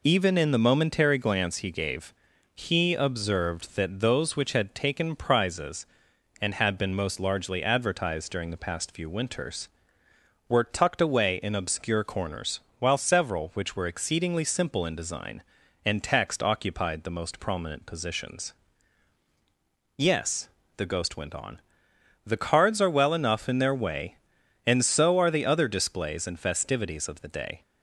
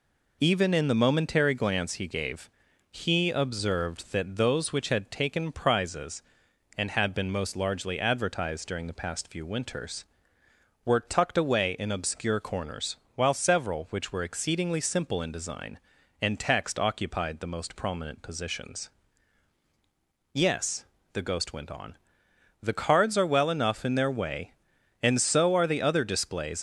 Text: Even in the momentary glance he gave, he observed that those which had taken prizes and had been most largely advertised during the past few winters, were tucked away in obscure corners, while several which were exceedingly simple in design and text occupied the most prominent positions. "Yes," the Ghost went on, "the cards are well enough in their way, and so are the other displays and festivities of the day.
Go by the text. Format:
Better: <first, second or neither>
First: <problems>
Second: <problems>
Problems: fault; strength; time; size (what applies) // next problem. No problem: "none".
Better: first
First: none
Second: stops before "and festivities of the day"; at 26.5 s